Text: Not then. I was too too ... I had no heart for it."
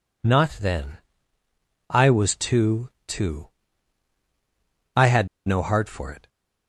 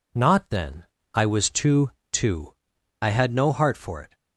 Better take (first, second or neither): second